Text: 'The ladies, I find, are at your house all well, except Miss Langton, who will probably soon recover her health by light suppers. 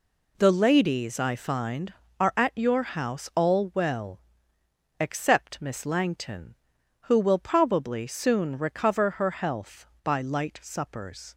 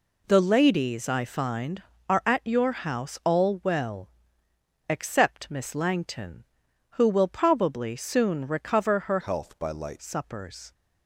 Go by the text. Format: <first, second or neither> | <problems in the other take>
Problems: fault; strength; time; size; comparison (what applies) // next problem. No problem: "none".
first | changes voice from "health" to "light"; from 9.2 to 10.0 s; 0.8 s long